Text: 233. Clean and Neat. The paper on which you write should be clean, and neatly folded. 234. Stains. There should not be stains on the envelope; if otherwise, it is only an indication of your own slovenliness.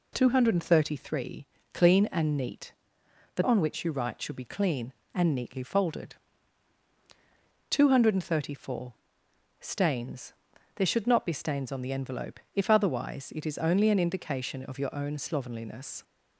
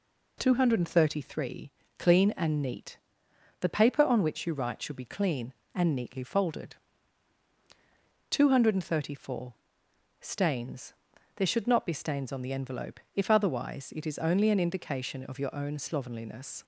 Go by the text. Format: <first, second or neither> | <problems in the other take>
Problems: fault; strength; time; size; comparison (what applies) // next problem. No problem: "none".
second | skips "paper"; at 3.4 s